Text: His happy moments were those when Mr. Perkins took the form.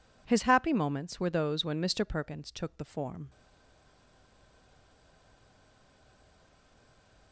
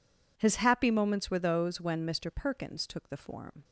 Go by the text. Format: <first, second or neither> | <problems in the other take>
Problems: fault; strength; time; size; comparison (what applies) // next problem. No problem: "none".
second | stays silent after the last word; strong; from 3.2 s on; 4.1 s long